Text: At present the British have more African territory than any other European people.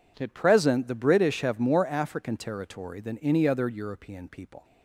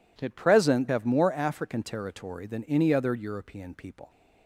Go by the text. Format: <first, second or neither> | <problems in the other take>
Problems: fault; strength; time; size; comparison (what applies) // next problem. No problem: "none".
first | skips "the British"; at 0.8 s